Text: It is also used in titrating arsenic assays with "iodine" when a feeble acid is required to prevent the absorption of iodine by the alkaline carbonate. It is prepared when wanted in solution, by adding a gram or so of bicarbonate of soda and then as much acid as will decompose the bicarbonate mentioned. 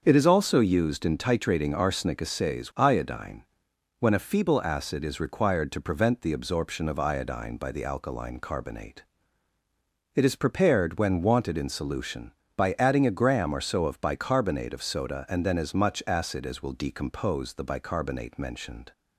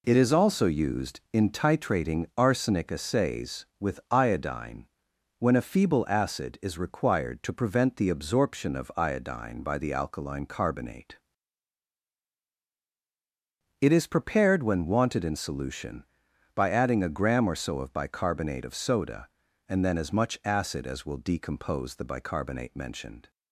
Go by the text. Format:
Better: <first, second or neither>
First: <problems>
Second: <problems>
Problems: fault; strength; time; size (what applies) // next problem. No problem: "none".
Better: second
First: starts louder than the rest; until 1.0 s; 6.5 dB // skips "with"; at 2.7 s // pauses between "iodine" and "when"; noticeable; at 3.4 s; 0.56 s long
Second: pauses between "iodine" and "when"; noticeable; at 4.8 s; 0.54 s long